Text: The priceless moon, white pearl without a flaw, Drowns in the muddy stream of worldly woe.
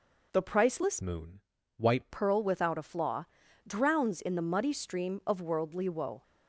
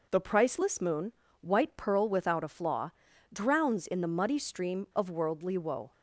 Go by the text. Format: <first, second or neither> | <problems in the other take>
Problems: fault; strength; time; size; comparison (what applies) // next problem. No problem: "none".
second | changes voice from "moon" to "white"; from 1.0 to 2.0 s; 1.0 s long